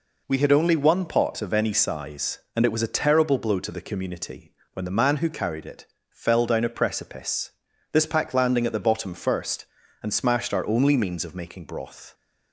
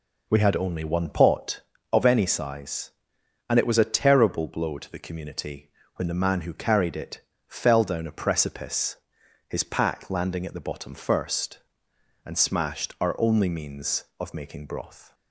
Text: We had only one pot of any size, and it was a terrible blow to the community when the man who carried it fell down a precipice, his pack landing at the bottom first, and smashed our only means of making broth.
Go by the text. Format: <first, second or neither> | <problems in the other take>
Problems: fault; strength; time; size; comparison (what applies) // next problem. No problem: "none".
second | pauses between "community" and "when"; slight; at 4.5 s; 0.18 s long; slight in the second // pauses between "it" and "fell"; slight; at 5.8 s; 0.24 s long; slight in the second // says "this" for "his"; at 7.9 s